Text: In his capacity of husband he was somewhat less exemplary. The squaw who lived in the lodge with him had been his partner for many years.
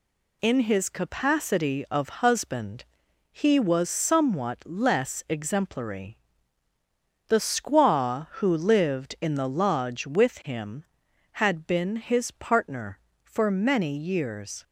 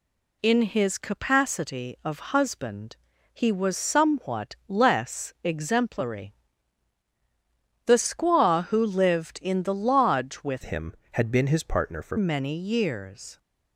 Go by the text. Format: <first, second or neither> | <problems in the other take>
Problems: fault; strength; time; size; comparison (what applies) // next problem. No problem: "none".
first | pauses between "husband" and "he"; at 2.9 s; 0.38 s long; noticeable in the first // changes voice from "him" to "for"; from 10.6 to 12.1 s; 1.5 s long